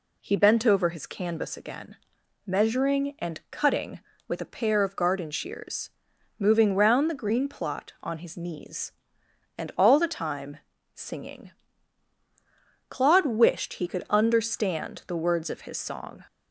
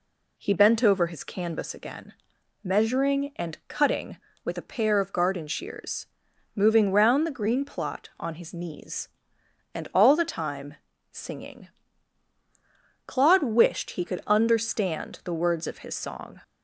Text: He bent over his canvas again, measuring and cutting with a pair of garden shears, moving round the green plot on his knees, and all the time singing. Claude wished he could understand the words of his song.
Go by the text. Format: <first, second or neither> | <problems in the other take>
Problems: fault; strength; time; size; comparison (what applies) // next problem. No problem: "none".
neither | pauses between "time" and "singing"; slight; the same in both